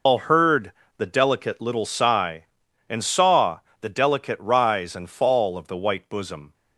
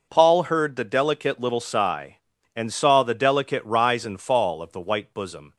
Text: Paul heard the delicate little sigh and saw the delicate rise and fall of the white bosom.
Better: second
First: loses the start of "Paul"; at 0.0 s; 100 ms // pauses between "heard" and "the"; slight; at 0.7 s; 0.26 s long // pauses between "saw" and "the"; slight; at 3.5 s; 0.22 s long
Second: none

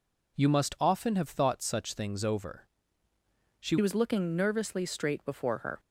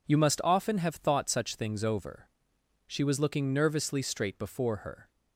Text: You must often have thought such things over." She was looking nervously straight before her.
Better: second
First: changes voice at "was"; from 3.7 s on; 2.0 s long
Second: none

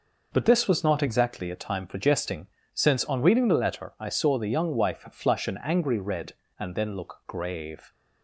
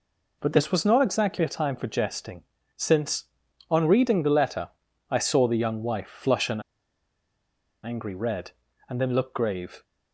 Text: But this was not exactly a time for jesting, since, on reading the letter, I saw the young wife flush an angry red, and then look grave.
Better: first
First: none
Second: pauses between "an" and "angry"; at 6.6 s; 1.2 s long

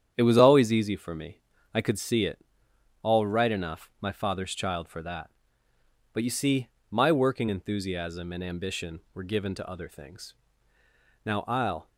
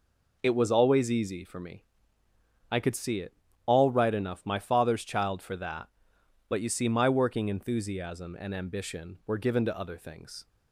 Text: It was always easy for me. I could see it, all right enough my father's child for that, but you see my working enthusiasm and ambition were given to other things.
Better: second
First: starts louder than the rest; strong; until 1.1 s; 9 dB // pauses between "see" and "my"; slight; at 6.6 s; 0.24 s long // goes on to say "Now I'll"; noticeable; from 11.2 s on; 0.62 s long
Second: none

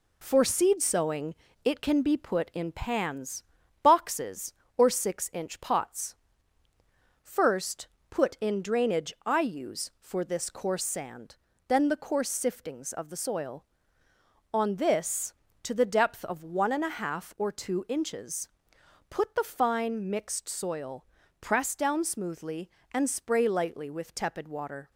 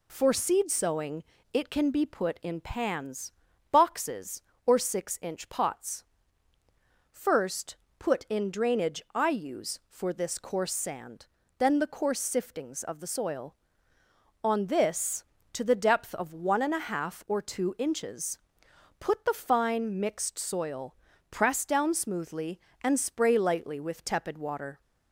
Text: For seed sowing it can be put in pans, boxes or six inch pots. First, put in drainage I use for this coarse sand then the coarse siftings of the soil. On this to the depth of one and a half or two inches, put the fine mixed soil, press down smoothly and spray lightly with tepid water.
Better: second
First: gets quieter; noticeable; throughout; 4 dB // pauses between "sowing" and "it"; slight; at 1.3 s; 0.30 s long // pauses between "sand" and "then"; slight; at 11.3 s; 0.32 s long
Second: pauses between "sowing" and "it"; slight; at 1.2 s; 0.30 s long // pauses between "sand" and "then"; slight; at 11.2 s; 0.32 s long

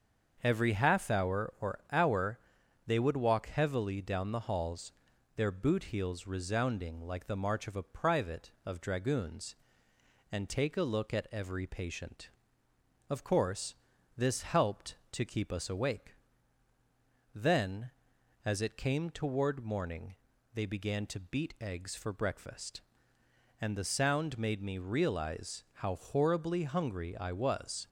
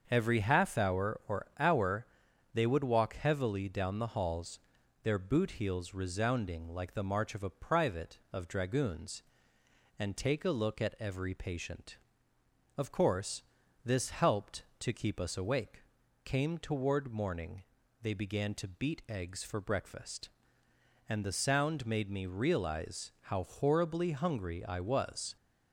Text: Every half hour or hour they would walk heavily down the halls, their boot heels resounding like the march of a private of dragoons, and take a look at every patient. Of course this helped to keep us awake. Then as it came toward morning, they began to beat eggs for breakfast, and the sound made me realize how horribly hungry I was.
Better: first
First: starts louder than the rest; until 1.4 s; 6.5 dB // pauses between "hour" and "they"; noticeable; at 2.3 s; 0.48 s long // pauses between "course" and "this"; at 13.7 s; 0.42 s long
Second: starts louder than the rest; until 1.1 s; 6.5 dB // pauses between "hour" and "they"; noticeable; at 2.0 s; 0.48 s long // pauses between "course" and "this"; at 13.4 s; 0.42 s long // skips "Then as it"; at 16.0 s

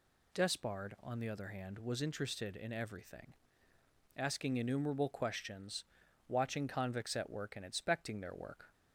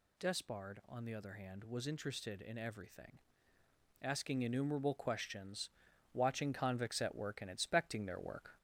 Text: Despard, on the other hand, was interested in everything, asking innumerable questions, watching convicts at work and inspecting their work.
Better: first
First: none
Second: gets louder; slight; throughout; 2.5 dB

